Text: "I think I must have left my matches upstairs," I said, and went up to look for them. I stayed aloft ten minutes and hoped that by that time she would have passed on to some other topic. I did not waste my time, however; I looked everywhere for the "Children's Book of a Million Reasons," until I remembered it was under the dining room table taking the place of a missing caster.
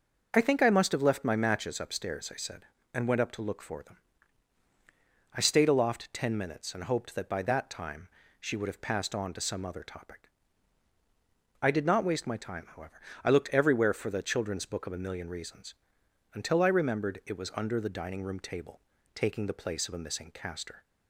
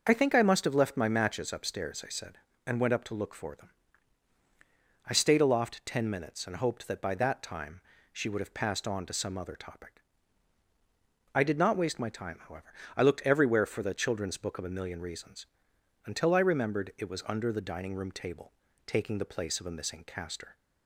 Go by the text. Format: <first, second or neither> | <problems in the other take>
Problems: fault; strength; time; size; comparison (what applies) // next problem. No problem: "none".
neither | starts louder than the rest; the same in both // pauses between "time" and "she"; slight; the same in both // pauses between "table" and "taking"; slight; the same in both